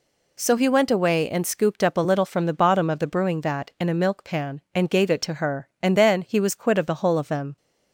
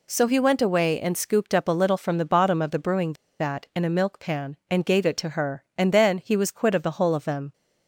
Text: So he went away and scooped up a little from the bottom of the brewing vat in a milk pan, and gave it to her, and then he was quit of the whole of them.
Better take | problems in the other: first | pauses between "brewing" and "vat"; slight; at 3.1 s; 0.26 s long

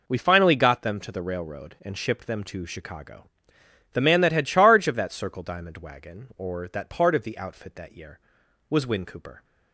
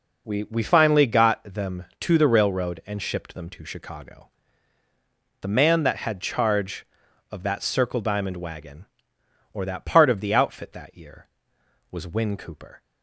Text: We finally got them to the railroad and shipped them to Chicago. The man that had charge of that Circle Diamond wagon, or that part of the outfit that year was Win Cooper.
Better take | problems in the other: first | says "We" twice; at 0.4 s

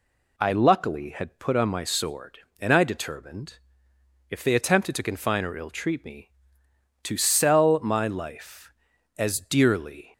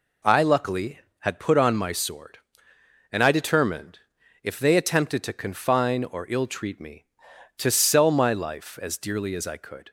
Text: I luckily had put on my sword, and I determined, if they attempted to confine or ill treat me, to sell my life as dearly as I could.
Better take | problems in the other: second | stops before "as I could"; at 10.1 s

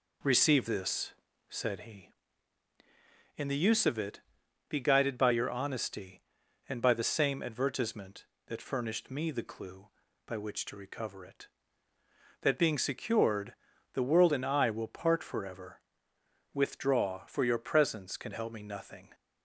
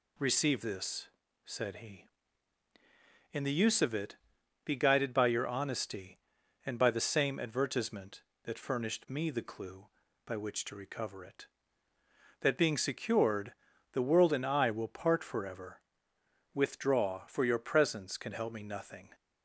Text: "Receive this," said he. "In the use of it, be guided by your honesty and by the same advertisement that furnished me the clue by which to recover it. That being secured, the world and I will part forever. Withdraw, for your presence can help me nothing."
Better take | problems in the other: second | starts louder than the rest; noticeable; until 1.9 s; 4 dB

